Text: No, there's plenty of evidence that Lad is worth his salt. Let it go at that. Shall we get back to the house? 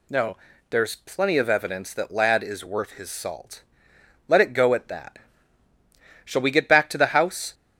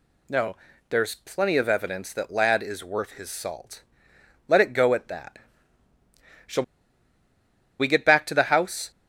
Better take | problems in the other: first | pauses between "Shall" and "we"; at 6.6 s; 1.1 s long

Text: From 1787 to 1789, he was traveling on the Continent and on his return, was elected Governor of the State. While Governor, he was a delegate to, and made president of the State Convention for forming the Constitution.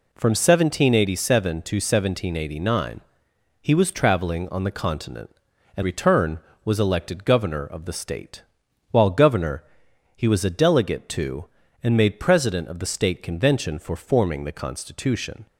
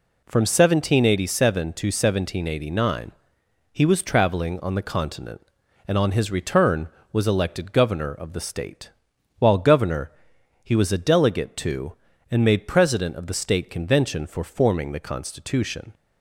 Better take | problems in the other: second | skips "on his"; at 5.8 s

